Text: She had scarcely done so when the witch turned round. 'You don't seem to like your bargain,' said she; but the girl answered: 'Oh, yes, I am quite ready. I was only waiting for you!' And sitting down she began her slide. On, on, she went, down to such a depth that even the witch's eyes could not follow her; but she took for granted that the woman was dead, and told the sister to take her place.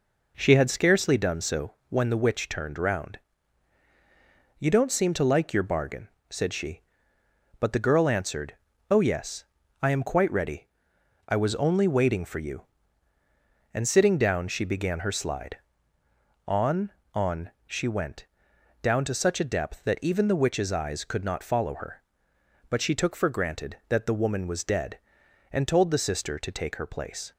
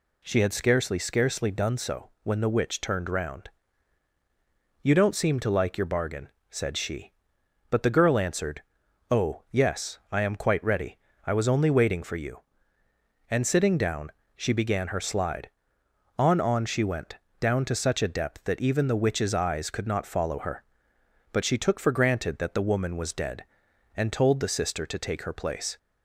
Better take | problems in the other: first | says "scarcely" twice; at 0.9 s // pauses between "down" and "she"; slight; at 14.1 s; 0.26 s long

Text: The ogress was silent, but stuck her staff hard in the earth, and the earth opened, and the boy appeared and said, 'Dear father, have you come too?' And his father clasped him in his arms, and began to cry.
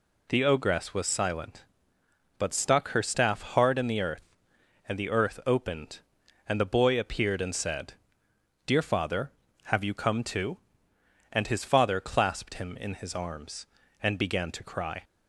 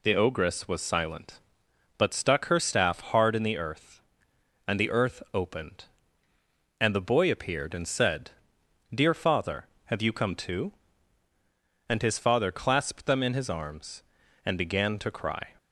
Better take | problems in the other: first | says "them" for "him"; at 13.0 s

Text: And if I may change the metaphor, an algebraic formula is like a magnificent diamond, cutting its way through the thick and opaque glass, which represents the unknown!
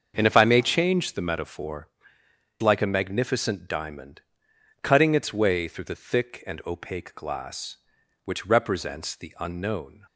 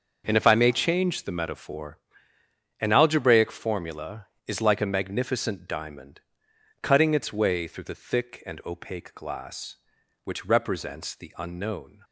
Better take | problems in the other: second | starts louder than the rest; until 1.1 s; 7 dB; also in the second // skips "an algebraic formula is"; at 2.2 s

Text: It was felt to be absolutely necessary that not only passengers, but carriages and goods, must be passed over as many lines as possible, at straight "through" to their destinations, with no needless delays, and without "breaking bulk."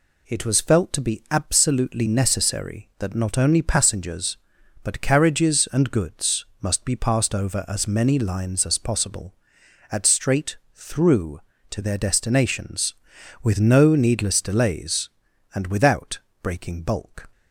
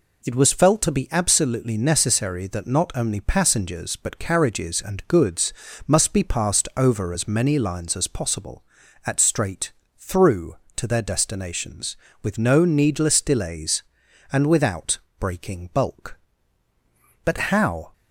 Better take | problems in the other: first | pauses between "straight" and "through"; slight; at 9.7 s; 0.26 s long; slight in the first // pauses between "without" and "breaking"; slight; at 14.9 s; 0.22 s long; slight in the first // goes on to say "But how"; noticeable; from 17.2 s on; 0.70 s long

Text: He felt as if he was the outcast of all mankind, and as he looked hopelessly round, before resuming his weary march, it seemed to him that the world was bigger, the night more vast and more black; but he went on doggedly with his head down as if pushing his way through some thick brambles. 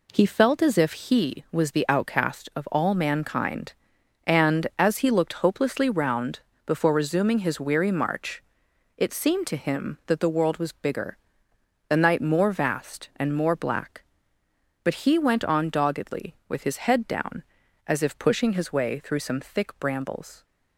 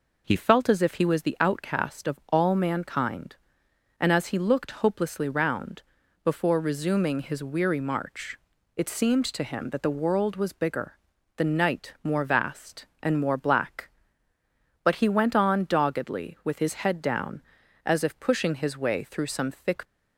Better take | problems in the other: first | stops before "brambles"; at 19.8 s

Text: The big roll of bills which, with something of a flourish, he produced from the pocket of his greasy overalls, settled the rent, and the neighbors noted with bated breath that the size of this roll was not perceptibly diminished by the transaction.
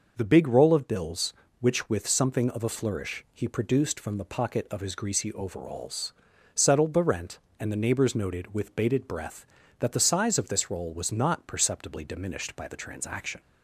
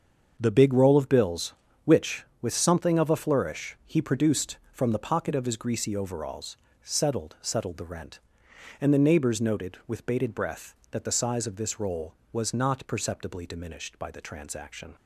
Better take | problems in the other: first | starts louder than the rest; until 1.3 s; 7 dB // says "settled" twice; at 7.4 s

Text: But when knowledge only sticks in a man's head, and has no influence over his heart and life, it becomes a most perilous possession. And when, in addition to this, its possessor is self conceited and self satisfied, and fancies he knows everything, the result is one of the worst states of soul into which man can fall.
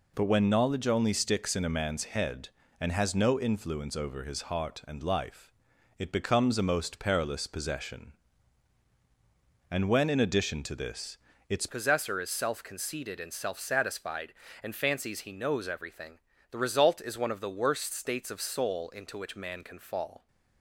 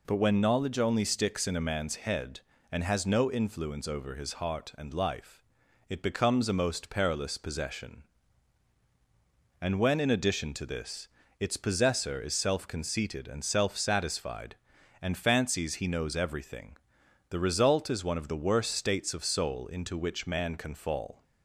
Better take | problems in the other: second | changes voice at "possessor"; from 11.6 s on; 8.6 s long

